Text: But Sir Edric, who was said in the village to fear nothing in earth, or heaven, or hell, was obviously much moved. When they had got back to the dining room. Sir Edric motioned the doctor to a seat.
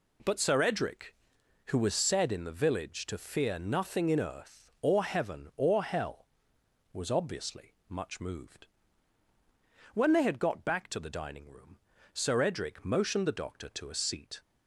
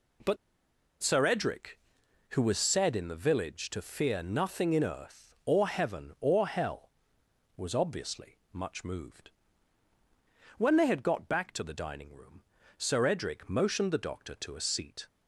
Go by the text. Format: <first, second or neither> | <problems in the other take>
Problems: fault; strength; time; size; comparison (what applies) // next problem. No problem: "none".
first | pauses between "But" and "Sir"; noticeable; at 0.3 s; 0.66 s long // pauses between "obviously" and "much"; slight; at 8.3 s; 0.16 s long; slight in the first